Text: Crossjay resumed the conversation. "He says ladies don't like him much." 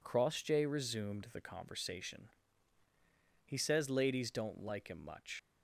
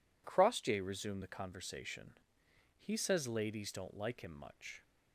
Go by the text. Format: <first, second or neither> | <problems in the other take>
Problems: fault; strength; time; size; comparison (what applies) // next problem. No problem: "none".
second | leaves "much" unfinished; at 5.3 s; 80 ms